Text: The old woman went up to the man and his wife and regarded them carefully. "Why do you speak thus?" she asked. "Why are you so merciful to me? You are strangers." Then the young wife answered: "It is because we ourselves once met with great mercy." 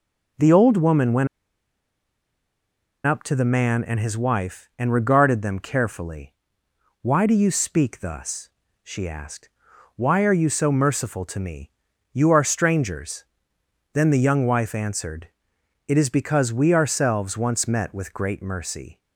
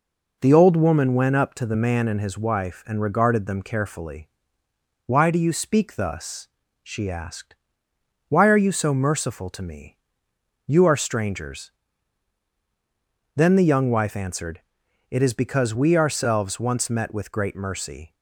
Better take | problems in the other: second | pauses between "went" and "up"; strong; at 1.2 s; 1.7 s long

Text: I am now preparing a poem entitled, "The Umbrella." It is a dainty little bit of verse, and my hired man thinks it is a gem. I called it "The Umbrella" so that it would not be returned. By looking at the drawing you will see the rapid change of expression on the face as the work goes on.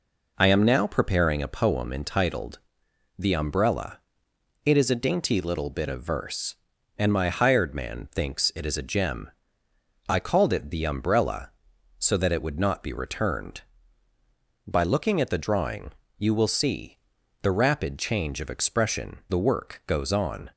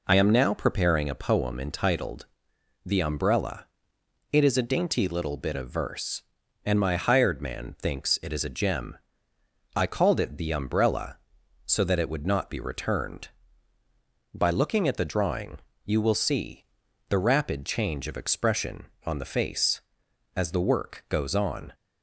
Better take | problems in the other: second | pauses between "drawing" and "you"; slight; at 15.9 s; 0.24 s long; slight in the second // pauses between "see" and "the"; at 16.9 s; 0.44 s long; also in the second // skips "on the face as"; at 19.2 s

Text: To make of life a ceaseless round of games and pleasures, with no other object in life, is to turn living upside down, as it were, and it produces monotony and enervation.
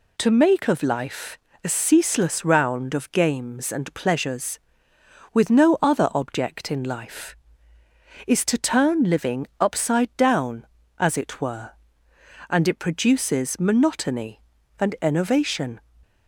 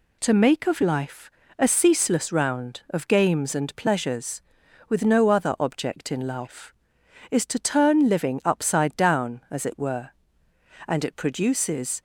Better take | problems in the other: first | pauses between "life" and "a"; slight; at 1.3 s; 0.28 s long; slight in the first // stops before "monotony and enervation"; at 11.9 s

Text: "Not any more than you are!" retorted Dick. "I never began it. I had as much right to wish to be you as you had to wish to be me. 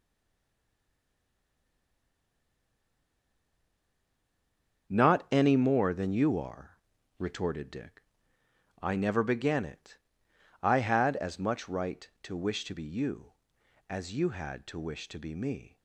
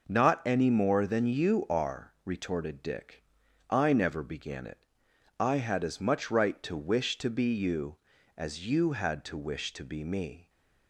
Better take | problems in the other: second | stays silent before the first word; strong; until 4.8 s; 4.8 s long // starts louder than the rest; until 5.9 s; 7 dB

